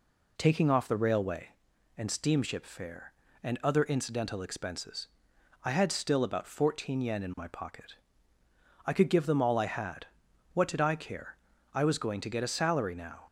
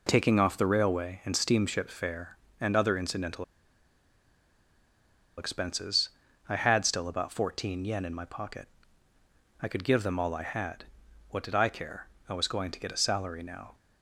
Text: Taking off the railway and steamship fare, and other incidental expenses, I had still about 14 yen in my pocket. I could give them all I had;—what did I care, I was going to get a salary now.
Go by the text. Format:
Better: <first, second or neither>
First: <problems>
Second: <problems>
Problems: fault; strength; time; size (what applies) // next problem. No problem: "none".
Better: first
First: none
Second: pauses between "incidental" and "expenses"; strong; at 3.4 s; 1.9 s long